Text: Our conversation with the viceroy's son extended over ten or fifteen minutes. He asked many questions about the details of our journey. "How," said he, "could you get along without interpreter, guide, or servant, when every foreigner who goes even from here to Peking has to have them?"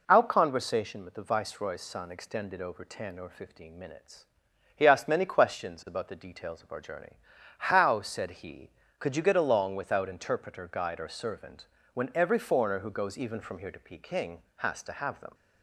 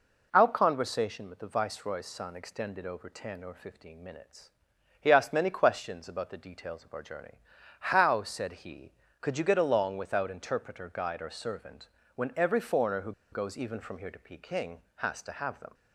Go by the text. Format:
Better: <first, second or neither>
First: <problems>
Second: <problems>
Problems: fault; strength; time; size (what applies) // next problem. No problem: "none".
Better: first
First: none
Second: pauses between "who" and "goes"; slight; at 13.1 s; 0.20 s long